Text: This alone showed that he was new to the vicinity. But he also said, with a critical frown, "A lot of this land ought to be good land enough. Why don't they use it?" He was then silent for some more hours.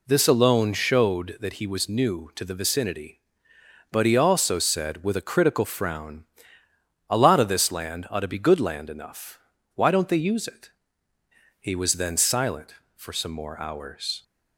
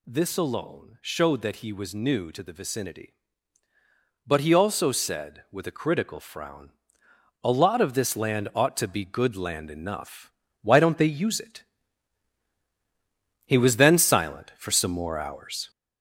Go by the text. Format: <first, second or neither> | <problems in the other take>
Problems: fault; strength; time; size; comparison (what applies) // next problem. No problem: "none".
first | gets louder; noticeable; throughout; 6 dB